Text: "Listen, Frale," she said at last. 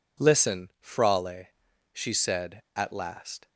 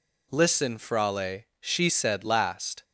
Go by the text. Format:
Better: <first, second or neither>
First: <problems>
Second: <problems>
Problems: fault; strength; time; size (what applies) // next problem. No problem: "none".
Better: first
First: none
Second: skips "at"; at 2.2 s